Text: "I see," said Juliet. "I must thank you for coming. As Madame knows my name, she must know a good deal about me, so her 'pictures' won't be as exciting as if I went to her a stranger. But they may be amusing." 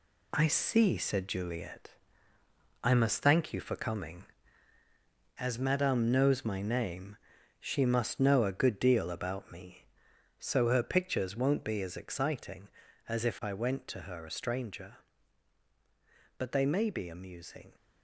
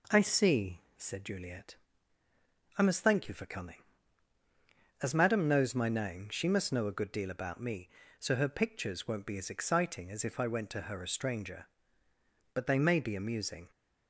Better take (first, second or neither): second